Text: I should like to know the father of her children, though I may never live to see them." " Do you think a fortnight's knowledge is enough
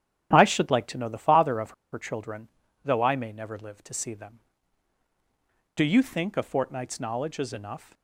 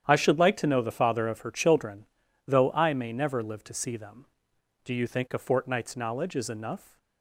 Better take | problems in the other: second | starts louder than the rest; strong; until 1.3 s; 11 dB; strong in the second // pauses between "of" and "her"; slight; at 1.7 s; 0.20 s long

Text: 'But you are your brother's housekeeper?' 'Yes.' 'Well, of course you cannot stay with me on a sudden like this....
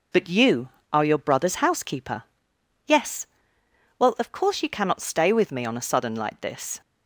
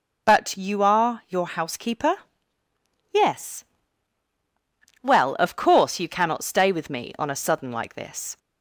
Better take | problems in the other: first | skips "brother's"; at 1.4 s

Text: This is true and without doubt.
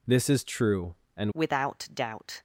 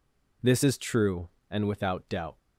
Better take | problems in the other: second | changes voice at "without"; from 1.3 s on; 1.1 s long

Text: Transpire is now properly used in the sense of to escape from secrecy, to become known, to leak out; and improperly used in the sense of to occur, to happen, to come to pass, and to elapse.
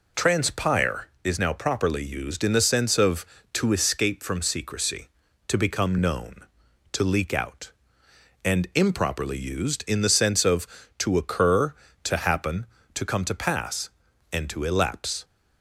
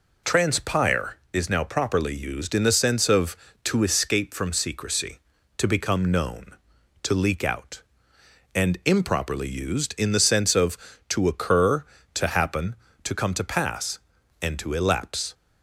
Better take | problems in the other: neither | none

